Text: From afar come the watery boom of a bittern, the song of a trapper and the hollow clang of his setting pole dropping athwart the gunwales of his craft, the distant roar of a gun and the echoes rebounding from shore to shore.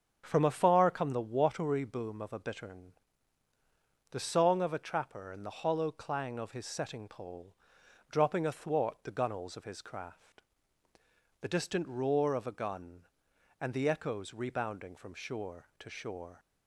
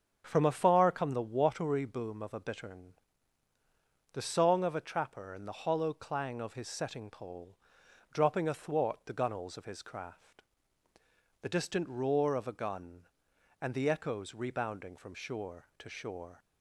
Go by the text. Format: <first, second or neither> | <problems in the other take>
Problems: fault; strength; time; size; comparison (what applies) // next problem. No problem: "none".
neither | starts louder than the rest; strong; the same in both // pauses between "pole" and "dropping"; noticeable; the same in both